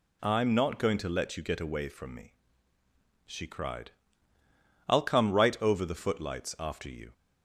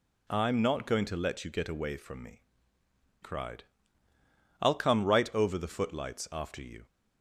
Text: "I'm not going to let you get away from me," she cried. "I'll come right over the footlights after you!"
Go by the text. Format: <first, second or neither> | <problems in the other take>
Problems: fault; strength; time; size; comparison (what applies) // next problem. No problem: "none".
first | skips "she"; at 2.8 s